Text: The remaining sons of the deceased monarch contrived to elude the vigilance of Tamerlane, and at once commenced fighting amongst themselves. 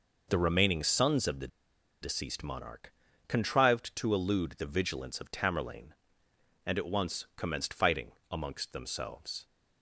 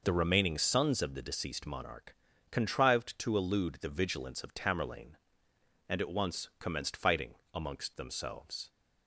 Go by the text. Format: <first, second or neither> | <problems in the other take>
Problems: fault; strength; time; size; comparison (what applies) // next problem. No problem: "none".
second | pauses between "the" and "deceased"; noticeable; at 1.4 s; 0.54 s long // pauses between "monarch" and "contrived"; slight; at 2.9 s; 0.36 s long; slight in the second // pauses between "fighting" and "amongst"; slight; at 8.1 s; 0.18 s long; slight in the second